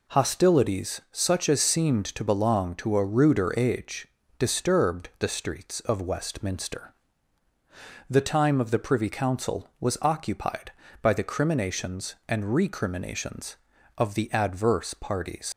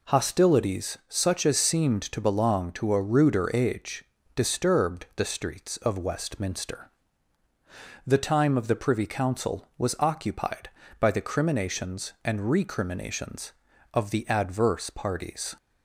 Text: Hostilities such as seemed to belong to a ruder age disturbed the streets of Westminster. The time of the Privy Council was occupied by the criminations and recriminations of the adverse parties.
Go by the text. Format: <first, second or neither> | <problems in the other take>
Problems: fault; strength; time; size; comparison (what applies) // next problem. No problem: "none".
second | pauses between "age" and "disturbed"; slight; at 4.0 s; 0.32 s long; slight in the second // leaves "parties" unfinished; at 15.5 s; 100 ms